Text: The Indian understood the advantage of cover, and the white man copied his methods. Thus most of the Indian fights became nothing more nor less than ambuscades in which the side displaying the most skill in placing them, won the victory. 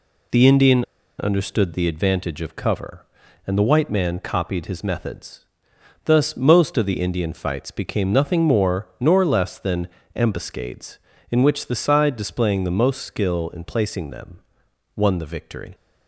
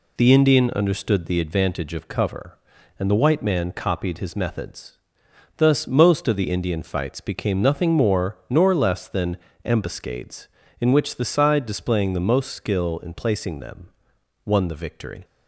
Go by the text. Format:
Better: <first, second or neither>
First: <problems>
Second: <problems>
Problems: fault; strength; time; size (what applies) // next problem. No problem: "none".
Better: second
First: pauses between "Indian" and "understood"; slight; at 0.8 s; 0.33 s long // pauses between "than" and "ambuscades"; slight; at 9.8 s; 0.28 s long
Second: pauses between "than" and "ambuscades"; slight; at 9.3 s; 0.28 s long